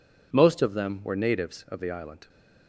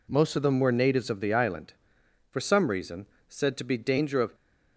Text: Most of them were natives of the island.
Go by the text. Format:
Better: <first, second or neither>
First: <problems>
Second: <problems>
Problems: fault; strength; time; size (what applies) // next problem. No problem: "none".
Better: first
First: none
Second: goes on to say "For some reason said to be danger of"; strong; from 2.3 s on; 2.0 s long